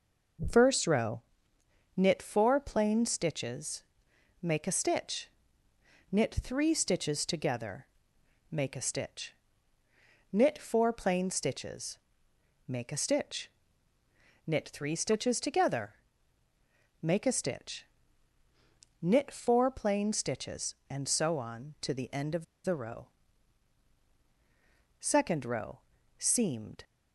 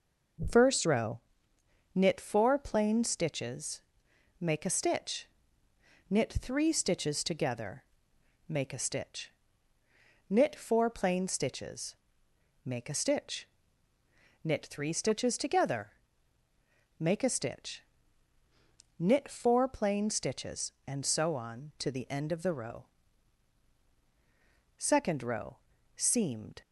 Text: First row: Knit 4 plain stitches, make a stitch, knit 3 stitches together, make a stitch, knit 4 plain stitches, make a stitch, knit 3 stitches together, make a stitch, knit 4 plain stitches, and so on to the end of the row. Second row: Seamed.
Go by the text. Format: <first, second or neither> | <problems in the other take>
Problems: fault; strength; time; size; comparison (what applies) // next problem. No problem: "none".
second | pauses between "of" and "the"; slight; at 22.4 s; 0.20 s long